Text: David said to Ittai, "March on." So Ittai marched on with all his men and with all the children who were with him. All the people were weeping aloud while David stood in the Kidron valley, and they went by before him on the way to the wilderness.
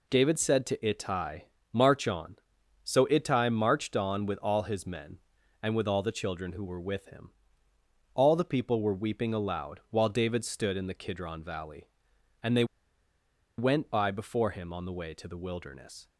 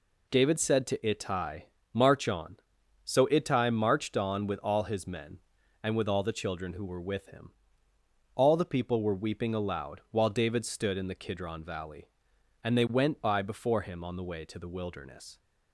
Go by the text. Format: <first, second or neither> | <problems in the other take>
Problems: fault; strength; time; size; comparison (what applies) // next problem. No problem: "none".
second | pauses between "they" and "went"; noticeable; at 12.6 s; 0.93 s long